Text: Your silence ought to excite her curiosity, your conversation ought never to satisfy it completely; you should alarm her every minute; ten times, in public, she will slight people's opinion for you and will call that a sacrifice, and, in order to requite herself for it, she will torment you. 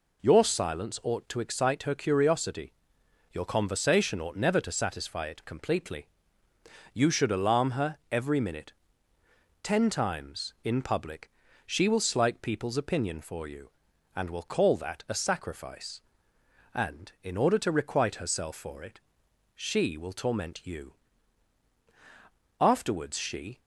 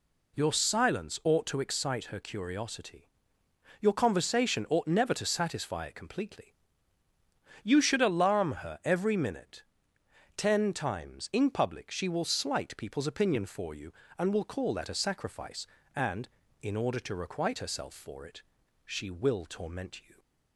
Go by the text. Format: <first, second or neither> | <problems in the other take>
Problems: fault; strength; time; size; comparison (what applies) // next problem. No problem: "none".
second | goes on to say "Afterwards she"; noticeable; from 22.5 s on; 1.0 s long